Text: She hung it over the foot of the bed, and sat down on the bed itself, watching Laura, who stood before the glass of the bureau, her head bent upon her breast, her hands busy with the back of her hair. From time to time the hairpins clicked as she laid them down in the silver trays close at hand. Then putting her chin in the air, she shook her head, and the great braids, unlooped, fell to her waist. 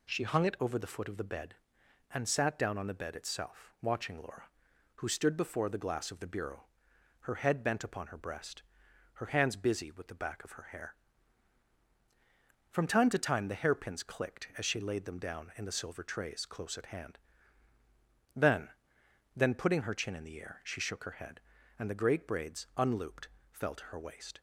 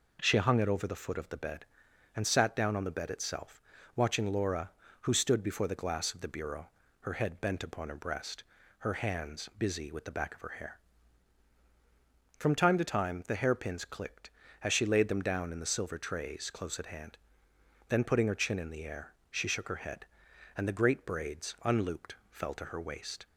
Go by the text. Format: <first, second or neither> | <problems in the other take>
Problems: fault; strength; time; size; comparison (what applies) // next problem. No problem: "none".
second | says "Then" twice; at 19.3 s